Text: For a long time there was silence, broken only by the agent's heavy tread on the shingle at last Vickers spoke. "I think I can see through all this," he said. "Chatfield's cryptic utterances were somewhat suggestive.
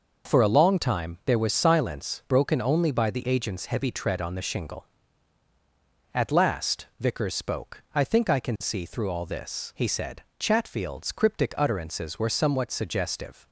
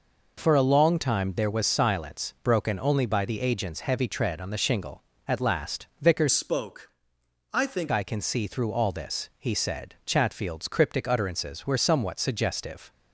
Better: first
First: none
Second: changes voice from "spoke" to "think"; from 6.3 to 7.9 s; 1.6 s long

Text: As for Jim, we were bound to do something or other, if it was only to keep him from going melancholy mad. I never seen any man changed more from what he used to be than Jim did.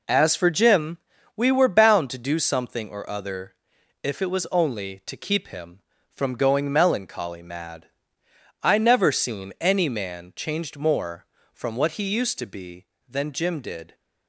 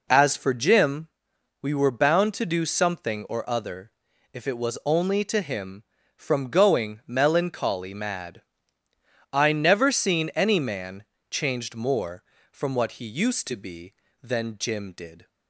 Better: first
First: none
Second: skips "keep"; at 5.4 s // pauses between "man" and "changed"; slight; at 11.0 s; 0.26 s long

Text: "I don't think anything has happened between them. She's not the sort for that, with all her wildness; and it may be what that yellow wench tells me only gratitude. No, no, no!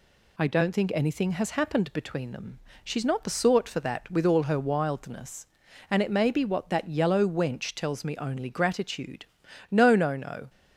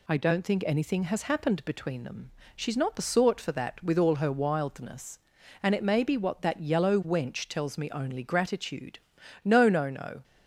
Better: neither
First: none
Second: none

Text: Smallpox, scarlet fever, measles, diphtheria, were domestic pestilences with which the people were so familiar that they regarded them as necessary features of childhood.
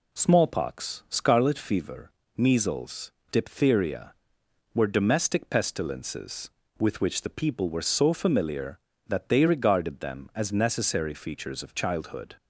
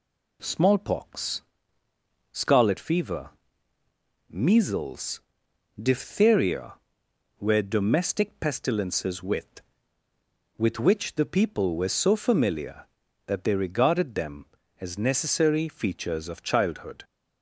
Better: first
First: none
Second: says "with" twice; at 10.5 s

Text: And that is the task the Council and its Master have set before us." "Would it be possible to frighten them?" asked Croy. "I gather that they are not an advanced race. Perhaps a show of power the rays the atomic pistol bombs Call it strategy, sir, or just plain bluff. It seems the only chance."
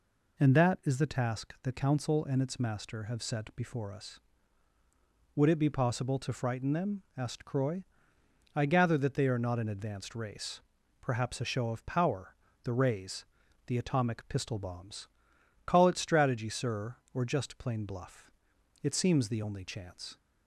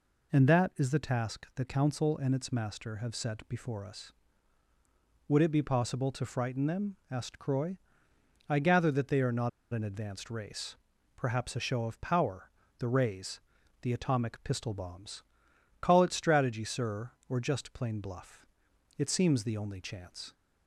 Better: first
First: pauses between "power" and "the"; slight; at 12.3 s; 0.30 s long // pauses between "rays" and "the"; at 13.2 s; 0.44 s long // pauses between "bombs" and "Call"; noticeable; at 15.0 s; 0.56 s long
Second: pauses between "not" and "an"; slight; at 9.4 s; 0.23 s long // pauses between "power" and "the"; slight; at 12.4 s; 0.30 s long // pauses between "rays" and "the"; at 13.3 s; 0.44 s long // pauses between "bombs" and "Call"; noticeable; at 15.2 s; 0.56 s long

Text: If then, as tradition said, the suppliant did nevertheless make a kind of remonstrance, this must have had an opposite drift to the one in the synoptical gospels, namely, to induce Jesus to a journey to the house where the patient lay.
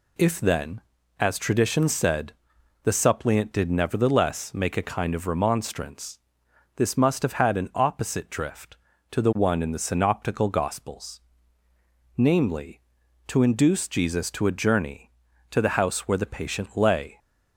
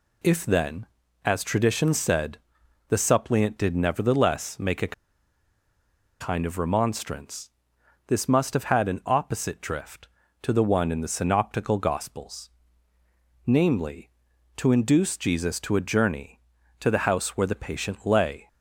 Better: first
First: none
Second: pauses between "a" and "kind"; strong; at 4.9 s; 1.2 s long

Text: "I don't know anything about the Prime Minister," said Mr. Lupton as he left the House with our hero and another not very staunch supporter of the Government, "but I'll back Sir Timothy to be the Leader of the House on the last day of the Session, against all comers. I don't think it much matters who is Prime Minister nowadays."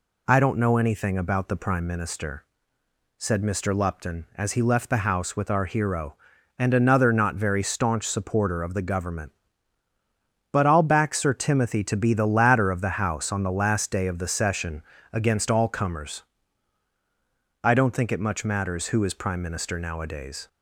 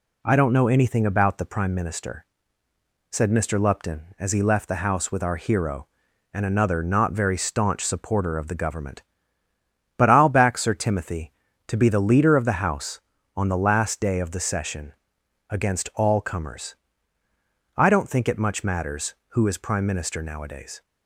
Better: second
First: says "Ladder" for "Leader"; at 12.2 s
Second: none

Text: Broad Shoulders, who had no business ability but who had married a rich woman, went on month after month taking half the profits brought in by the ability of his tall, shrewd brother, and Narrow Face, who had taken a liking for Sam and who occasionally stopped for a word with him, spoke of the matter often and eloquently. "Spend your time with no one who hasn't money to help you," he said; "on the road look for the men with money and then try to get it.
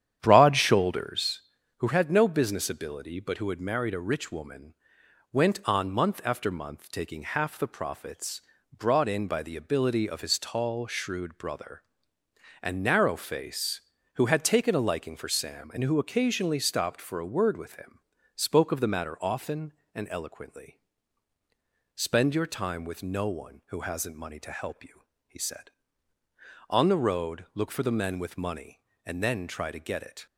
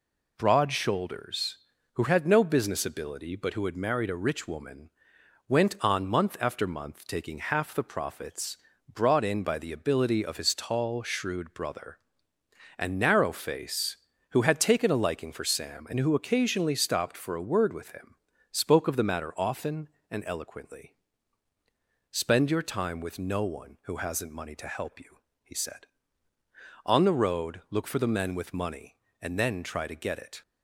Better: second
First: starts louder than the rest; strong; until 1.4 s; 9.5 dB // pauses between "profits" and "brought"; slight; at 8.4 s; 0.34 s long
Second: pauses between "profits" and "brought"; slight; at 8.5 s; 0.34 s long

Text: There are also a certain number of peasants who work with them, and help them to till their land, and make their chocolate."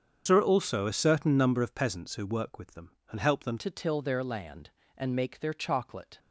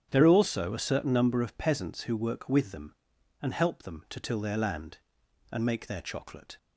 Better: second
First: starts louder than the rest; strong; until 1.2 s; 7.5 dB // changes voice at "to"; from 3.5 s on; 2.6 s long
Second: starts louder than the rest; strong; until 1.1 s; 8 dB

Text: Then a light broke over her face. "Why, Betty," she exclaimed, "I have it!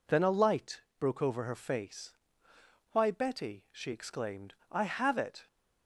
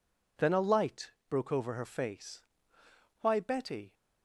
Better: first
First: pauses between "light" and "broke"; slight; at 0.8 s; 0.18 s long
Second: pauses between "light" and "broke"; slight; at 1.1 s; 0.18 s long // stops before "she exclaimed I have it"; at 3.9 s

